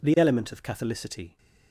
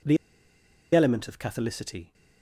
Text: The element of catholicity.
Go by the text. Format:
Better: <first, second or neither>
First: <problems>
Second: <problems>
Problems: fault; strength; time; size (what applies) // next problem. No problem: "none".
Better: first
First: none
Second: pauses between "The" and "element"; noticeable; at 0.1 s; 0.78 s long